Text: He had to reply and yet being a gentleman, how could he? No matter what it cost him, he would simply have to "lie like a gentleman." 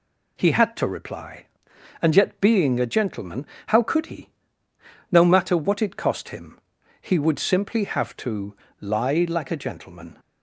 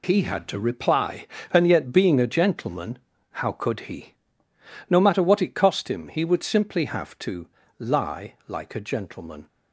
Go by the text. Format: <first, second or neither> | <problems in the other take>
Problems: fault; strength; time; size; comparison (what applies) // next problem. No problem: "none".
neither | pauses between "to" and "lie"; slight; the same in both